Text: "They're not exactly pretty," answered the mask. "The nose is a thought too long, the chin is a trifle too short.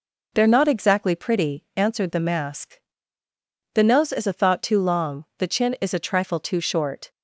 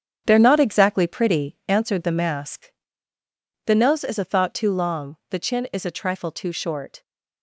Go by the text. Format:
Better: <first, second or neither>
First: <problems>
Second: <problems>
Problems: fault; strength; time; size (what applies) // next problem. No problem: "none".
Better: first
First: none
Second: gets quieter; strong; throughout; 9 dB